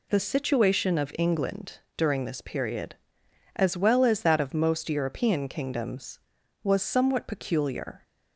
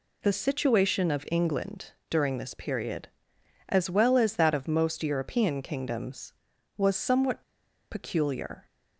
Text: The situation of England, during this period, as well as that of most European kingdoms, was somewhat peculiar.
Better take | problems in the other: first | pauses between "somewhat" and "peculiar"; noticeable; at 7.4 s; 0.50 s long

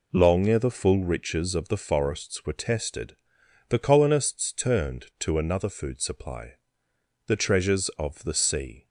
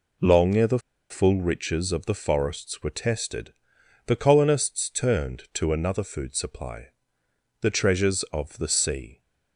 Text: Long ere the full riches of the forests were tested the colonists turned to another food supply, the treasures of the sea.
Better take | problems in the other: first | pauses between "the" and "full"; slight; at 0.7 s; 0.31 s long // pauses between "tested" and "the"; noticeable; at 3.5 s; 0.54 s long; noticeable in the first

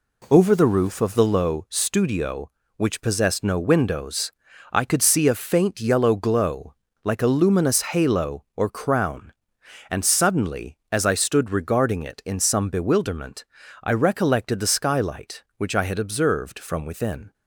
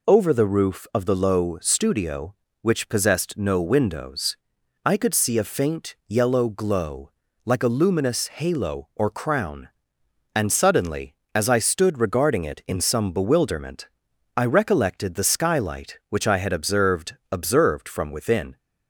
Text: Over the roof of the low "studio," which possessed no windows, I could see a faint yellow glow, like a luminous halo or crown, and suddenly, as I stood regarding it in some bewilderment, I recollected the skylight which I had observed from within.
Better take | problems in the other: first | says "observed" twice; at 17.3 s

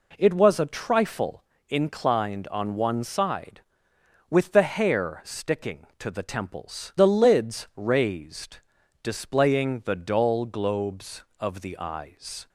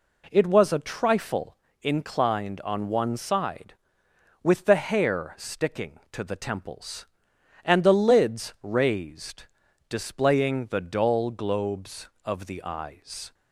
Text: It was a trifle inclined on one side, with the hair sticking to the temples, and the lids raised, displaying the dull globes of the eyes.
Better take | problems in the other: second | pauses between "trifle" and "inclined"; slight; at 1.4 s; 0.24 s long; slight in the second // skips "and"; at 6.9 s

